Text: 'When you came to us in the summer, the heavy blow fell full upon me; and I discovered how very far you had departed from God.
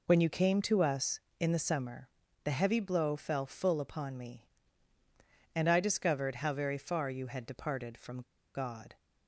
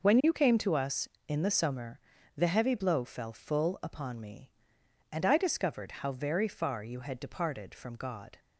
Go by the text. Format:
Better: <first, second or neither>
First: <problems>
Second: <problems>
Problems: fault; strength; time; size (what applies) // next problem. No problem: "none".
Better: second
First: pauses between "from" and "God"; slight; at 8.1 s; 0.35 s long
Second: none